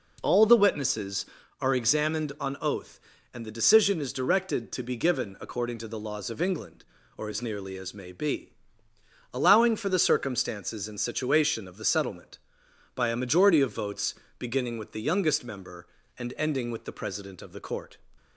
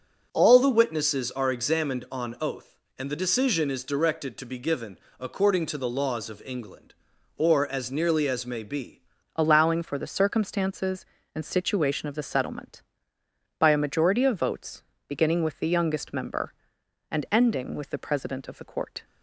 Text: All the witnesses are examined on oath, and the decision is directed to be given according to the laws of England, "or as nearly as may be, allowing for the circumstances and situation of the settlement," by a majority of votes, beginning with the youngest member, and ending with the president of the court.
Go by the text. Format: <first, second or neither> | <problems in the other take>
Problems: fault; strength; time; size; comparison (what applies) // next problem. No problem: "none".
first | pauses between "given" and "according"; slight; at 4.9 s; 0.22 s long // changes voice at "allowing"; from 9.3 s on; 9.7 s long